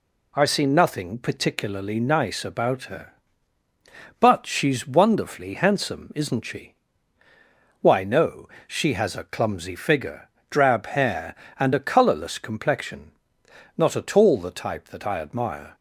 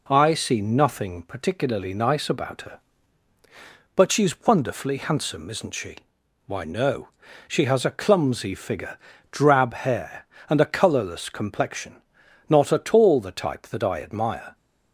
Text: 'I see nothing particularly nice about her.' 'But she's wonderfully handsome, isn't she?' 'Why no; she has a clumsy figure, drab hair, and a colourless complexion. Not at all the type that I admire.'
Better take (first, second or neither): neither